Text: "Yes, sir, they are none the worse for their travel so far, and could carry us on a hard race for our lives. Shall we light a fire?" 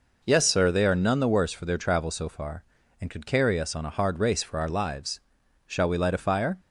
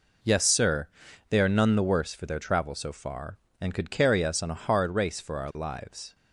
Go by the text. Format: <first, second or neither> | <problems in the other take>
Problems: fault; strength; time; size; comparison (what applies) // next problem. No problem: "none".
first | stops before "Shall we light a fire"; at 6.1 s